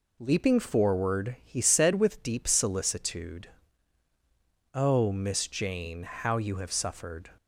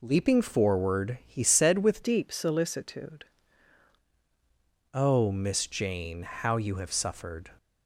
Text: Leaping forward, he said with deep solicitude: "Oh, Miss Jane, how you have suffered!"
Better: first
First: none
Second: changes voice from "deep" to "solicitude"; from 2.0 to 3.2 s; 1.2 s long

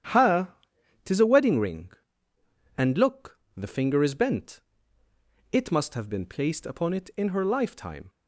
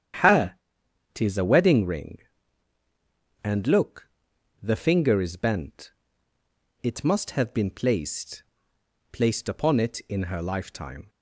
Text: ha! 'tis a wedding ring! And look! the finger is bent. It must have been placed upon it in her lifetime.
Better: first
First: starts louder than the rest; strong; until 1.5 s; 9.5 dB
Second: starts louder than the rest; strong; until 1.7 s; 9.5 dB // says "placed" twice; at 9.1 s

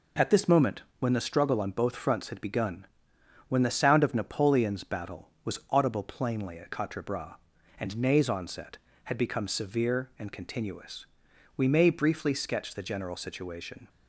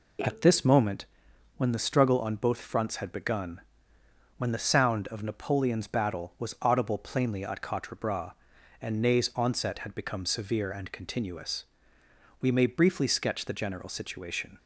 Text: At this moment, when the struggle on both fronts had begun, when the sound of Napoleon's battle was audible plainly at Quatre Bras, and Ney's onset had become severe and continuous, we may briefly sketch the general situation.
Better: neither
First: none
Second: none

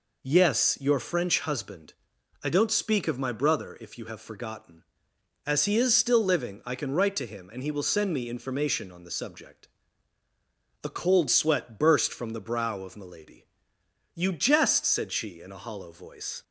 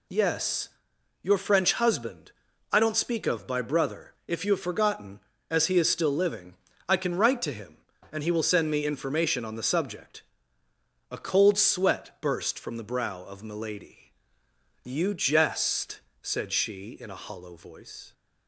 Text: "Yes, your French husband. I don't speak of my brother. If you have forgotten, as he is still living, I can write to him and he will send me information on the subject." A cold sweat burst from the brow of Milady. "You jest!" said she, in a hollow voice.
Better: first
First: none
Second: says "by" for "my"; at 3.4 s

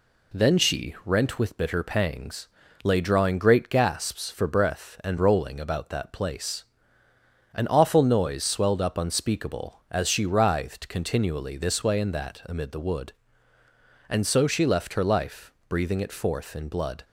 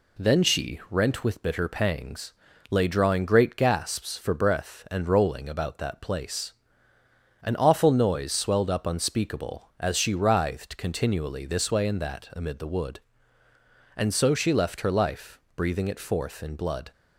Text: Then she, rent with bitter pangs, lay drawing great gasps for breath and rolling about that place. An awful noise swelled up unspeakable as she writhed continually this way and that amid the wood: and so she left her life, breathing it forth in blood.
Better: neither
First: none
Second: none

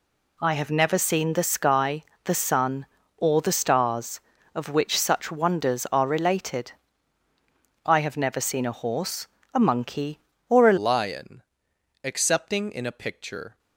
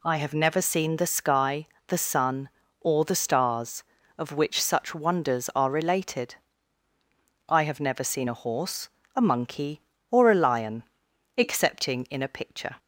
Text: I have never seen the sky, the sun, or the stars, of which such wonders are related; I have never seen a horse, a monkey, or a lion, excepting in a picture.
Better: second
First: changes voice at "lion"; from 10.7 s on; 2.8 s long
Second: none

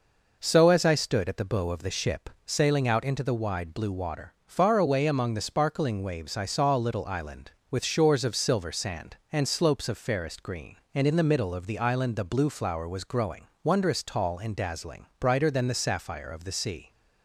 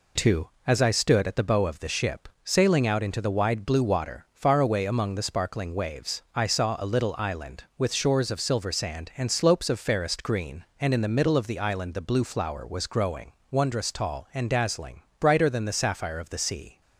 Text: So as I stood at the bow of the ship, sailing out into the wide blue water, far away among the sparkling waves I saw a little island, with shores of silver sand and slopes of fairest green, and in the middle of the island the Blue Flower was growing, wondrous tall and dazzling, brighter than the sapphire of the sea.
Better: first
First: none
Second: says "Too" for "So"; at 0.1 s

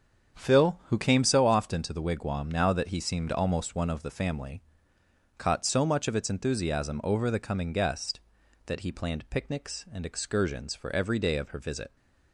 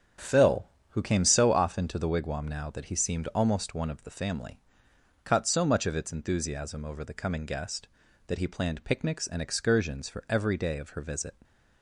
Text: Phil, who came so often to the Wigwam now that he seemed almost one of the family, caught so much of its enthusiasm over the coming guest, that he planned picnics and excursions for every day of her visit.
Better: neither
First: starts louder than the rest; strong; until 1.4 s; 7.5 dB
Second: starts louder than the rest; strong; until 1.4 s; 8 dB

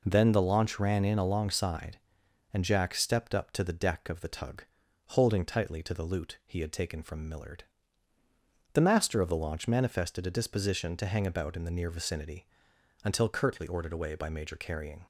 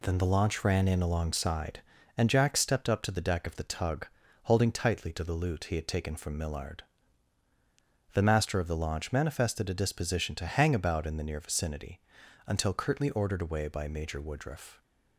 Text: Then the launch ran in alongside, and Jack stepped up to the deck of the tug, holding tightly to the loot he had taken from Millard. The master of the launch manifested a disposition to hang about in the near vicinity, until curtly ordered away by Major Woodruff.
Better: second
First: says "Carrying" for "Woodruff"; at 14.5 s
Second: none

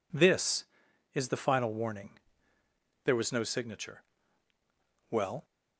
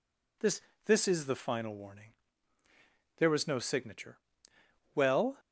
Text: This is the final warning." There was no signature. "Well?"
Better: first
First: none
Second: says "This" twice; at 0.8 s

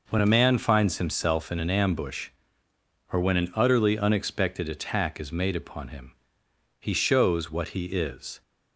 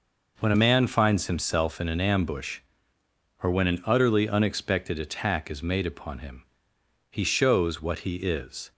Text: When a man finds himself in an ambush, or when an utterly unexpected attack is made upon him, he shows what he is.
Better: neither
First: none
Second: none

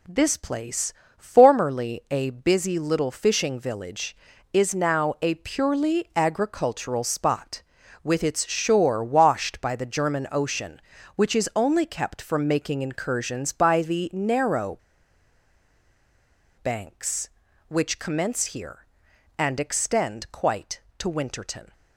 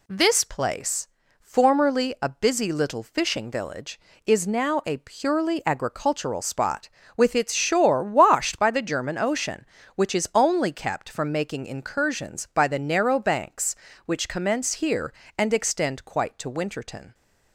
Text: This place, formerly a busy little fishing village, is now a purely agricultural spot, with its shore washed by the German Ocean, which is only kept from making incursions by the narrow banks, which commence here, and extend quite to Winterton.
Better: second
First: pauses between "narrow" and "banks"; strong; at 14.7 s; 1.8 s long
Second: none

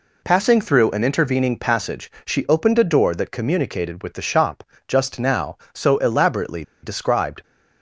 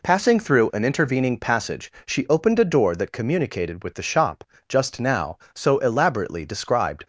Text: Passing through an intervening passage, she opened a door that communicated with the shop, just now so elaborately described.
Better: second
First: pauses between "elaborately" and "described"; slight; at 6.6 s; 0.20 s long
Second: none

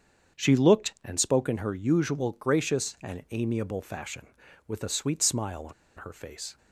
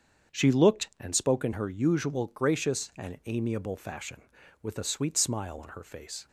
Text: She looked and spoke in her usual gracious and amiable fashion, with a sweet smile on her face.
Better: second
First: starts louder than the rest; strong; until 1.4 s; 7.5 dB // pauses between "on" and "her"; slight; at 5.7 s; 0.25 s long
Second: starts louder than the rest; strong; until 1.4 s; 7.5 dB

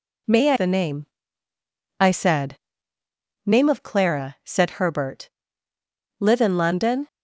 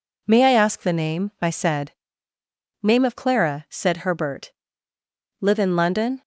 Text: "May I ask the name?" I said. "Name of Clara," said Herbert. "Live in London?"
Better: second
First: skips "ask"; at 0.5 s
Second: none

